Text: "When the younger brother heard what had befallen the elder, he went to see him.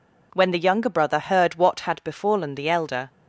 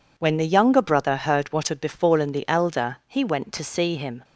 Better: second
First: stops before "he went to see him"; at 3.0 s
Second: none

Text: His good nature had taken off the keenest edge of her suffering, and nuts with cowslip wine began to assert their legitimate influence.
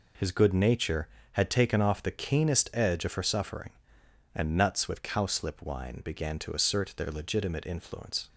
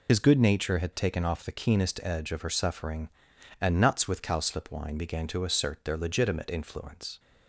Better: first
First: none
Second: loses the start of "His"; at 0.0 s; 75 ms

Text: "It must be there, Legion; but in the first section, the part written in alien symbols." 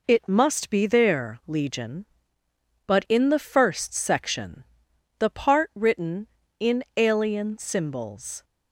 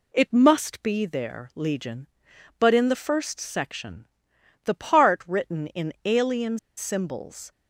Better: first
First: none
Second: pauses between "alien" and "symbols"; slight; at 6.5 s; 0.18 s long

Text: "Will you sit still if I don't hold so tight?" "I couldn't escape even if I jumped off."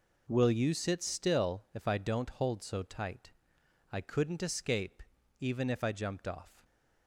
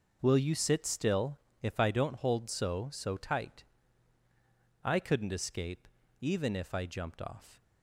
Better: first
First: pauses between "escape" and "even"; at 5.0 s; 0.38 s long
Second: pauses between "still" and "if"; slight; at 1.3 s; 0.22 s long // says "so" twice; at 2.9 s // pauses between "escape" and "even"; slight; at 5.8 s; 0.32 s long

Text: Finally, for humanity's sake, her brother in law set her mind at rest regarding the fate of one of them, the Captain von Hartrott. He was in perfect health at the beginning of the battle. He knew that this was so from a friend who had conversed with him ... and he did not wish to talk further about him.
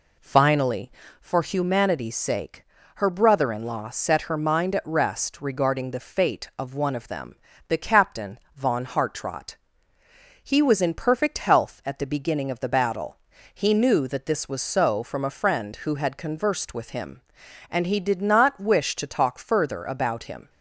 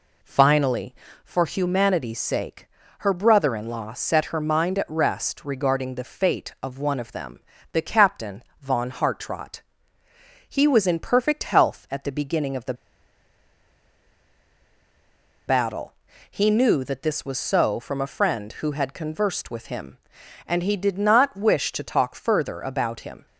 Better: first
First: pauses between "Captain" and "von"; slight; at 8.3 s; 0.16 s long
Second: pauses between "Captain" and "von"; slight; at 8.4 s; 0.18 s long // pauses between "the" and "battle"; strong; at 12.7 s; 2.7 s long

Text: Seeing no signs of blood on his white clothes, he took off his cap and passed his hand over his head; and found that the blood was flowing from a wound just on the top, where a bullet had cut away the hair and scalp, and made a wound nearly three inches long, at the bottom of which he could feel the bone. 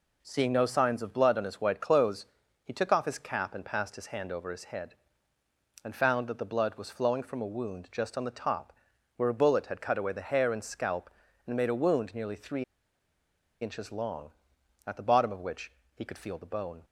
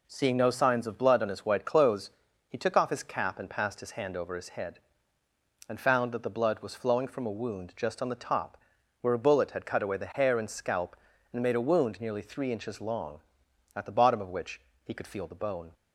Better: second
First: pauses between "three" and "inches"; at 12.6 s; 0.99 s long // pauses between "which" and "he"; slight; at 15.7 s; 0.24 s long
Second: pauses between "which" and "he"; slight; at 14.6 s; 0.24 s long

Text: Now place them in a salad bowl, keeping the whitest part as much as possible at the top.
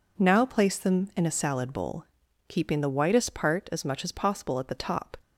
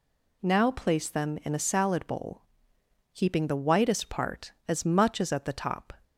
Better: first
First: none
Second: skips "possible"; at 5.3 s

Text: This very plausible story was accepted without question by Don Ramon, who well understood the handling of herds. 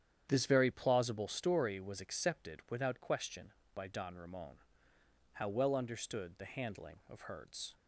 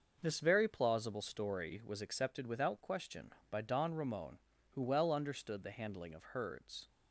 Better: second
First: starts louder than the rest; strong; until 1.3 s; 9 dB // says "how" for "who"; at 5.3 s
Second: none

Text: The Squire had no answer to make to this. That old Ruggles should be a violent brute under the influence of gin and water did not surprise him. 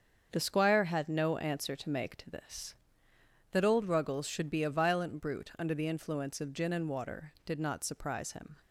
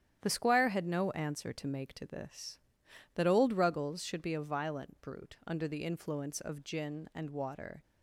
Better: first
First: starts louder than the rest; strong; until 1.3 s; 7 dB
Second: starts louder than the rest; strong; until 1.2 s; 10 dB // stops before "did not surprise him"; at 7.8 s

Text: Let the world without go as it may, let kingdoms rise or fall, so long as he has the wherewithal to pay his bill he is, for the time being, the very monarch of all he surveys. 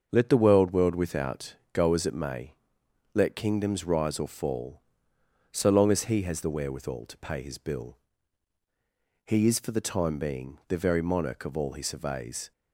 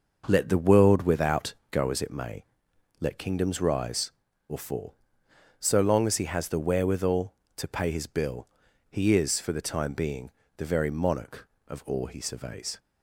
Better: second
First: starts louder than the rest; until 1.1 s; 6.5 dB // says "world" twice; at 0.7 s // pauses between "without" and "go"; slight; at 1.5 s; 0.18 s long // pauses between "bill" and "he"; strong; at 7.9 s; 1.3 s long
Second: pauses between "without" and "go"; slight; at 1.5 s; 0.18 s long // pauses between "bill" and "he"; at 8.4 s; 0.42 s long

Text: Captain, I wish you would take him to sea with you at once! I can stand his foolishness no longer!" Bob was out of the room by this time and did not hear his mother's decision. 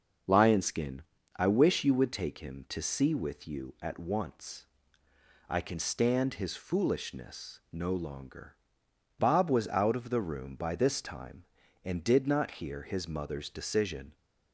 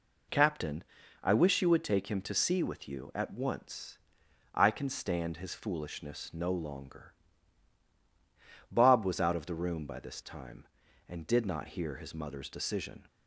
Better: second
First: says "Lionskin" for "Captain"; at 0.2 s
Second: none

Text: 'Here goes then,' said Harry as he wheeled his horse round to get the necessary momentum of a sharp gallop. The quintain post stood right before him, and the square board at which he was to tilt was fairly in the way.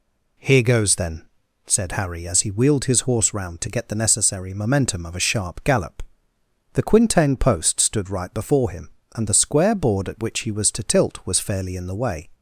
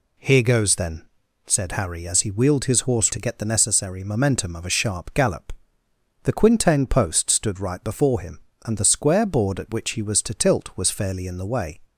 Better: first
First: none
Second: skips "round"; at 3.1 s

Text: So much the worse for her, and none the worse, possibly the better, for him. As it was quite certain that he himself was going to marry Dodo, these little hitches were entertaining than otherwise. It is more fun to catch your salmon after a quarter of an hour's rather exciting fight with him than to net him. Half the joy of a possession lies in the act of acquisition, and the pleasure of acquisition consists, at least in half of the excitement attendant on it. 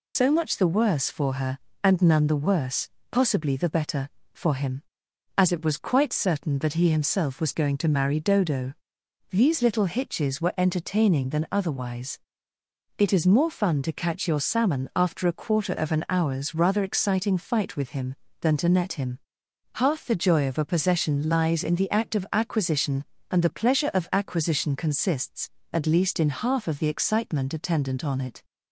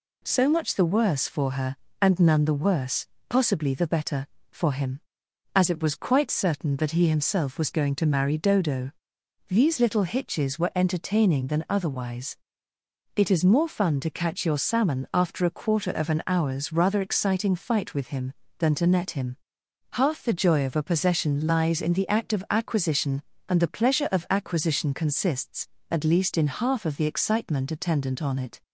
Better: second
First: loses the start of "So"; at 0.1 s; 90 ms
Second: none

